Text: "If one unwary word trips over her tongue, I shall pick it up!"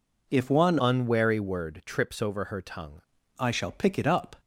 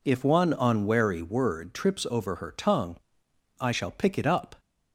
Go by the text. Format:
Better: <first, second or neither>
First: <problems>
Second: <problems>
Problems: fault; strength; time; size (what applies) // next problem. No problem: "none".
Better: second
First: changes voice from "unwary" to "tongue"; from 0.8 to 3.0 s; 2.2 s long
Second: none